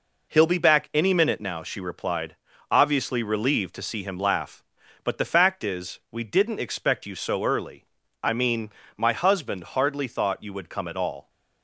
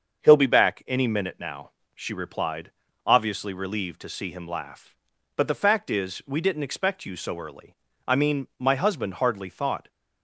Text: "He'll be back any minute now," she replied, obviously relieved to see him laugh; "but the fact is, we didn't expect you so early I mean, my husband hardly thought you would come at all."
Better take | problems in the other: first | starts louder than the rest; until 1.2 s; 6.5 dB // pauses between "early" and "I"; slight; at 7.7 s; 0.31 s long; also in the first // stops before "you would come at all"; at 9.8 s

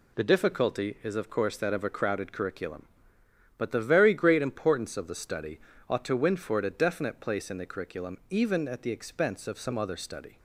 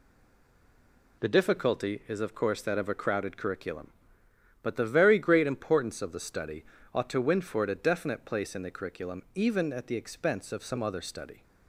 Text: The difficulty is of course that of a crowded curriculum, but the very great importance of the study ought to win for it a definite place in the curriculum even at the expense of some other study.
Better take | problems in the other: first | stays silent before the first word; noticeable; until 1.2 s; 1.2 s long // pauses between "study" and "ought"; slight; at 6.6 s; 0.30 s long; slight in the first

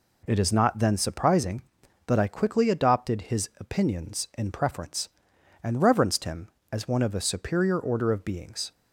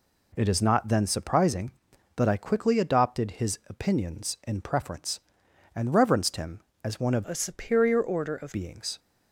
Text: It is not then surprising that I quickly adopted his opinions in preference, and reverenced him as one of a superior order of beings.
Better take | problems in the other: first | changes voice from "a" to "of"; from 7.2 to 8.5 s; 1.3 s long

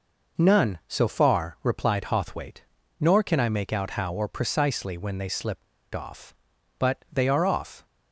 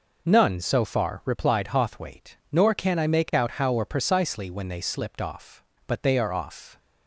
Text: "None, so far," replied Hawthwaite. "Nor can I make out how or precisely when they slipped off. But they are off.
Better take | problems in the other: second | pauses between "slipped" and "off"; slight; at 5.6 s; 0.30 s long

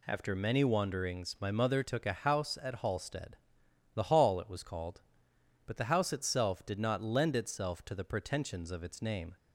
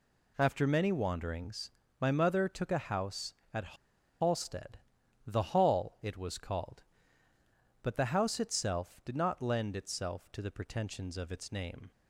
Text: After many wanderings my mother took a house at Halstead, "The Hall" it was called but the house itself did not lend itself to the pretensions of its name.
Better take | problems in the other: first | pauses between "wanderings" and "my"; slight; at 1.7 s; 0.30 s long // pauses between "at" and "Halstead"; at 3.7 s; 0.44 s long

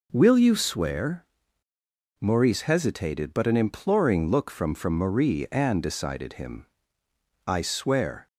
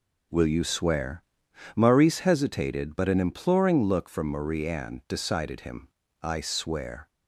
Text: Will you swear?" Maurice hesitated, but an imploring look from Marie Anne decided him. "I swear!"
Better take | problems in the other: second | says "from" twice; at 4.7 s

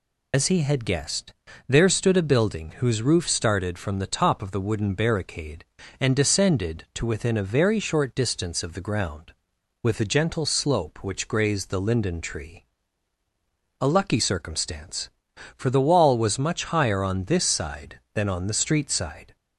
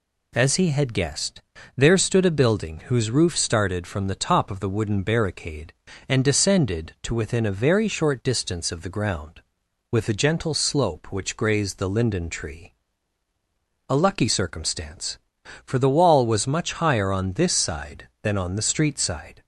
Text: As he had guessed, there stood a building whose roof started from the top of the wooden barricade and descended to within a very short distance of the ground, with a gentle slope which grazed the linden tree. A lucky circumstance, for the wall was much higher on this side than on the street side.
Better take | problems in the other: second | loses the start of "As"; at 0.3 s; 95 ms

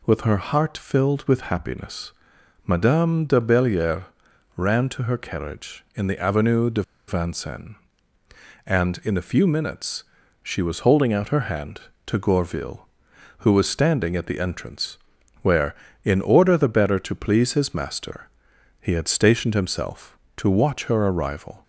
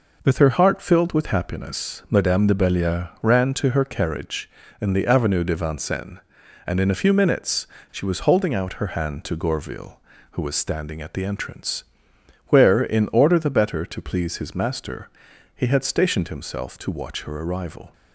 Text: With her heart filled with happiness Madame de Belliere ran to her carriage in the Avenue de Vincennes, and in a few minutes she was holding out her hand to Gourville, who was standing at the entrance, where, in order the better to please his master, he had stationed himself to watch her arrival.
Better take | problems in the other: second | pauses between "happiness" and "Madame"; noticeable; at 2.1 s; 0.54 s long // pauses between "Belliere" and "ran"; noticeable; at 4.0 s; 0.52 s long // pauses between "de" and "Vincennes"; slight; at 6.8 s; 0.26 s long // pauses between "minutes" and "she"; at 10.0 s; 0.40 s long; slight in the second

